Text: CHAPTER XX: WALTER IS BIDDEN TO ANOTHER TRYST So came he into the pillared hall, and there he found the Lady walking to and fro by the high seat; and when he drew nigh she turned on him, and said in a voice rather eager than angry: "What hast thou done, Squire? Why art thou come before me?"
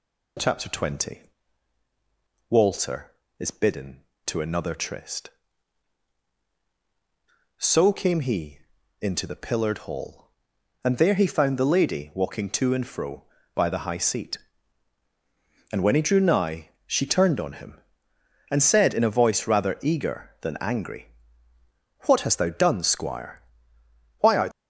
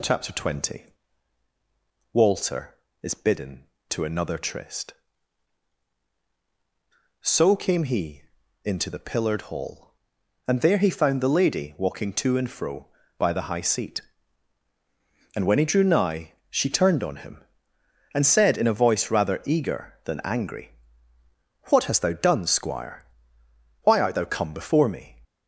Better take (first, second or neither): second